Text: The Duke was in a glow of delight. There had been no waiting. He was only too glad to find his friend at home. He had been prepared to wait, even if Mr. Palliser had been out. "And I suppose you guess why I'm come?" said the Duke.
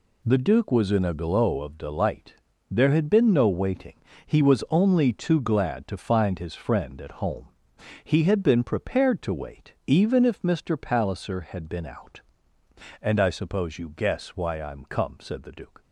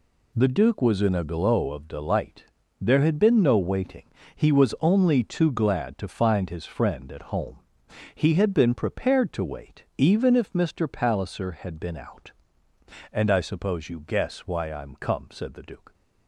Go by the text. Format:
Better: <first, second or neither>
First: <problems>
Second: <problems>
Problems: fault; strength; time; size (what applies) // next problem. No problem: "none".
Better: neither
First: none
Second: none